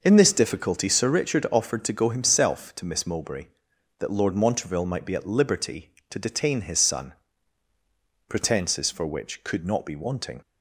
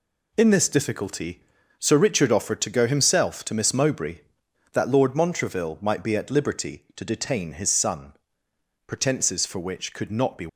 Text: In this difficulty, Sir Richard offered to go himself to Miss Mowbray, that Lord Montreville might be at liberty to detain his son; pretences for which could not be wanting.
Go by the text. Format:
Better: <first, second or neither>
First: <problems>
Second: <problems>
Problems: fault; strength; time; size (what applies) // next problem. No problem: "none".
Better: first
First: none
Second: stops before "wanting"; at 10.4 s